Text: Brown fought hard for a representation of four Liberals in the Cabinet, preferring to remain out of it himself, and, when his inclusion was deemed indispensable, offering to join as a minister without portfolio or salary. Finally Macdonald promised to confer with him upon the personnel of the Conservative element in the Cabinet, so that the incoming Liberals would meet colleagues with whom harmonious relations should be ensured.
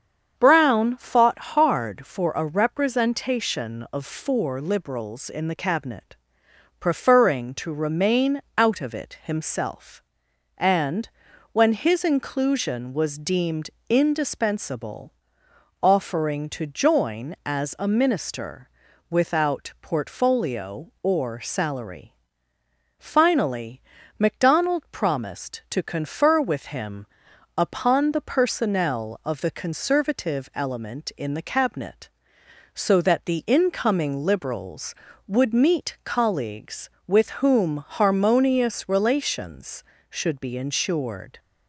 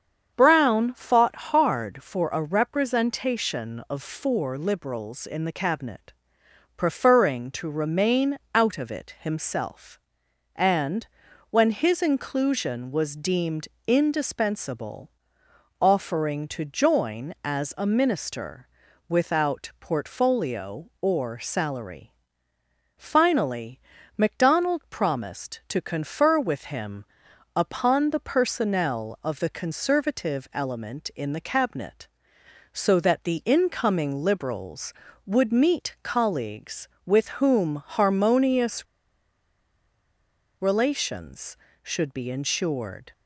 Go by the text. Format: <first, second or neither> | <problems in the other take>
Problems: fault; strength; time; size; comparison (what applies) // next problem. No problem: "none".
first | starts louder than the rest; strong; until 1.3 s; 7.5 dB; strong in the first // pauses between "fought" and "hard"; slight; at 1.3 s; 0.18 s long; slight in the first // pauses between "remain" and "out"; slight; at 8.3 s; 0.16 s long; slight in the first // pauses between "deemed" and "indispensable"; slight; at 13.6 s; 0.18 s long; slight in the first // pauses between "minister" and "without"; at 18.6 s; 0.40 s long; also in the first // pauses between "Finally" and "Macdonald"; at 23.7 s; 0.38 s long; also in the first // pauses between "him" and "upon"; noticeable; at 27.0 s; 0.50 s long; noticeable in the first // pauses between "harmonious" and "relations"; strong; at 38.8 s; 1.7 s long